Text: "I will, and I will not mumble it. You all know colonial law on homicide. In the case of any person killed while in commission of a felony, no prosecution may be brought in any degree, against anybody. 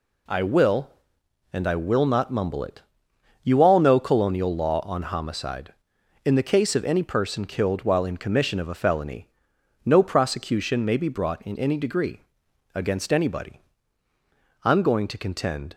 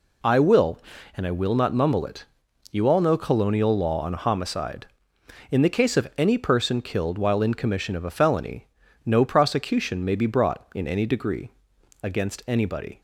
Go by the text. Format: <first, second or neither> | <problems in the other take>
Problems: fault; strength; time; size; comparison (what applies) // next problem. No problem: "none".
second | goes on to say "I'm going to contend"; noticeable; from 14.6 s on; 1.1 s long